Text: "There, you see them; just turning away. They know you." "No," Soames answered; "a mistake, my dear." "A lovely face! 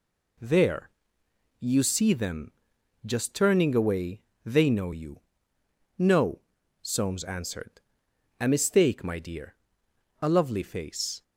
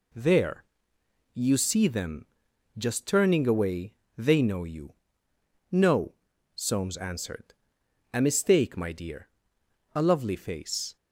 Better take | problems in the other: neither | none

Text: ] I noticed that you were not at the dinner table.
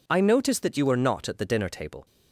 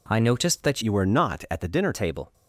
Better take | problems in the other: first | changes voice from "you" to "dinner"; from 0.8 to 1.9 s; 1.1 s long

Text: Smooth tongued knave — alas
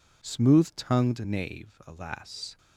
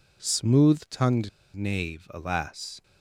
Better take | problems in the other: first | pauses between "tongued" and "knave"; slight; at 1.2 s; 0.26 s long

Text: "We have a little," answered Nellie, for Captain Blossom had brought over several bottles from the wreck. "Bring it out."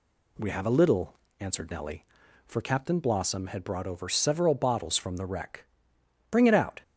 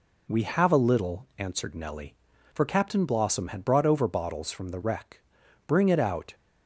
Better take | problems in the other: first | skips "several"; at 4.0 s

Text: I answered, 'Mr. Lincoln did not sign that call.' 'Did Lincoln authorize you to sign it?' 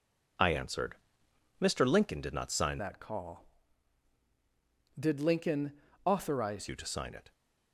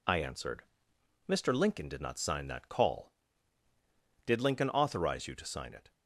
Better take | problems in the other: second | changes voice from "that" to "authorize"; from 2.7 to 6.6 s; 3.9 s long // pauses between "Lincoln" and "authorize"; slight; at 5.7 s; 0.30 s long

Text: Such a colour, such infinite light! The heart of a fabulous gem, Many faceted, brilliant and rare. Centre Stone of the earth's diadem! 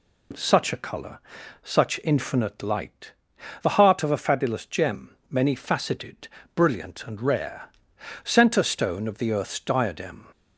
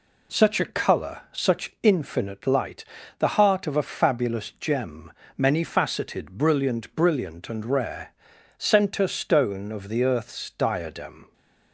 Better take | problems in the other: first | says "brilliant" twice; at 6.9 s

